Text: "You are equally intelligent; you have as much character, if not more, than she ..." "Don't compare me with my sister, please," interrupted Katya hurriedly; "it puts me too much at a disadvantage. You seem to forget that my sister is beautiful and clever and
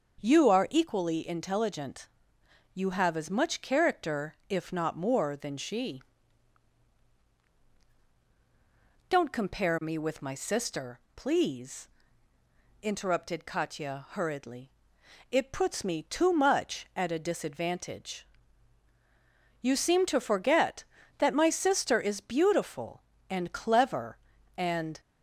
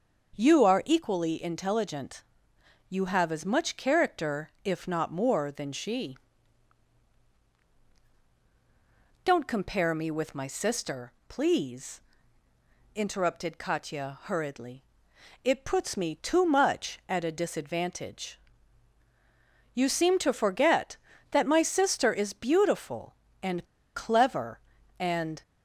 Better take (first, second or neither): first